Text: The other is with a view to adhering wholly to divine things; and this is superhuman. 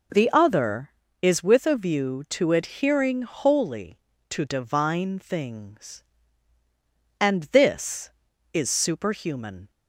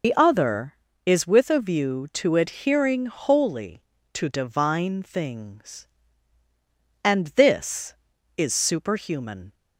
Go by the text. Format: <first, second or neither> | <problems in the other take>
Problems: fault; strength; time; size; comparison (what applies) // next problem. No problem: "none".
first | loses the start of "The"; at 0.0 s; 90 ms